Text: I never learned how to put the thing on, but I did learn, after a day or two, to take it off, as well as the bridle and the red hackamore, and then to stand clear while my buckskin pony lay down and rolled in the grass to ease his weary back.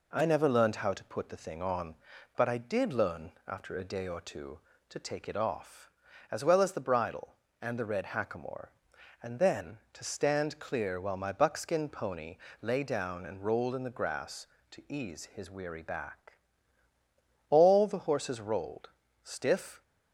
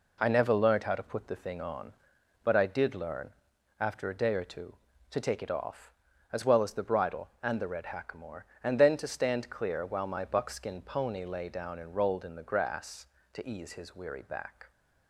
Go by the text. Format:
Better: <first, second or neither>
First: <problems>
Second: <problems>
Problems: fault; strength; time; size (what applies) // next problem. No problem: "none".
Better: second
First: pauses between "pony" and "lay"; slight; at 12.3 s; 0.24 s long // goes on to say "All the horses rolled stiff"; strong; from 17.4 s on; 2.3 s long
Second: none